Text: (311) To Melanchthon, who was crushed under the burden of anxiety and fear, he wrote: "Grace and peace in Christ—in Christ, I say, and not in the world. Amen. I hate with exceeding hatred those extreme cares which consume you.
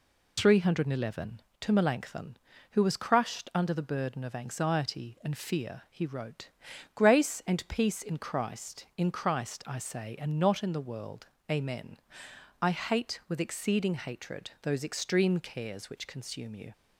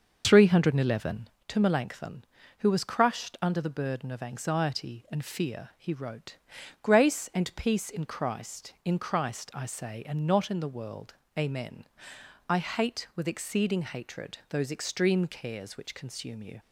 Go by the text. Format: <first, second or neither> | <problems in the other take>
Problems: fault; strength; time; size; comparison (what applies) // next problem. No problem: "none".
first | starts louder than the rest; noticeable; until 1.4 s; 6 dB